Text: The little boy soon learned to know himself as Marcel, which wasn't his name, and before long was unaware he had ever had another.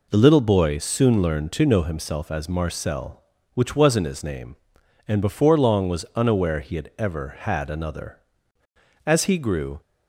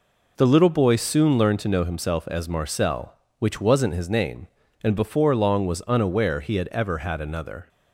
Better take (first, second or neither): second